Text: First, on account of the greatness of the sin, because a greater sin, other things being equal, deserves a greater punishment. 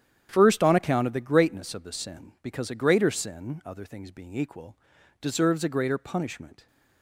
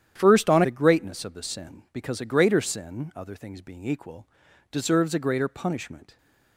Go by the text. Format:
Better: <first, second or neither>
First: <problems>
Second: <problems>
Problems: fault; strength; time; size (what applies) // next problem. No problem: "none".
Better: first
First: starts louder than the rest; strong; until 1.3 s; 9.5 dB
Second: starts louder than the rest; strong; until 1.2 s; 10 dB // skips "account of"; at 0.6 s